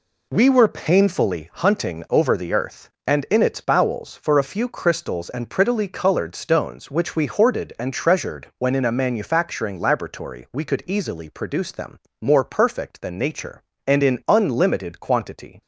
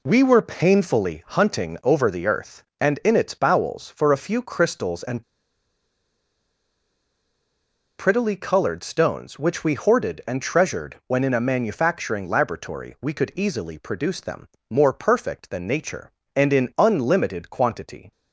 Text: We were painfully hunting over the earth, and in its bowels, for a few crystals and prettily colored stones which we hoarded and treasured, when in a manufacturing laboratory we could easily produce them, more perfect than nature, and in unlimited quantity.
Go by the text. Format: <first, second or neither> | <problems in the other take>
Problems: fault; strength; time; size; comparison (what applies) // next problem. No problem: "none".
first | pauses between "and" and "prettily"; strong; at 5.2 s; 2.7 s long